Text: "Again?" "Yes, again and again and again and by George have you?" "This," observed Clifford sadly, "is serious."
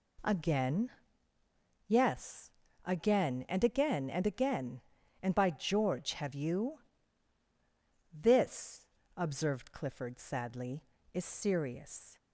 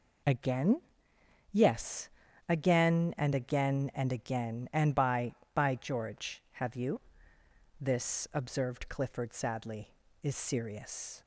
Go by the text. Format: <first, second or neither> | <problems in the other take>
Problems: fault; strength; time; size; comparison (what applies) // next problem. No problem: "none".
first | says "by" twice; at 5.5 s